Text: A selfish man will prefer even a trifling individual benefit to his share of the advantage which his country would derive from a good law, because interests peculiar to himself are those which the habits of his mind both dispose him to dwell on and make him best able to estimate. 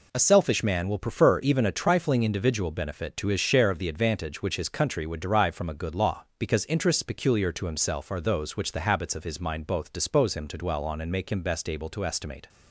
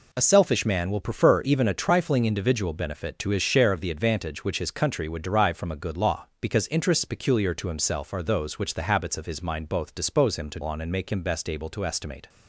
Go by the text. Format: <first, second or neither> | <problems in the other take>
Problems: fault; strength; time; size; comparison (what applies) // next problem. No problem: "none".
first | skips "dwell"; at 10.6 s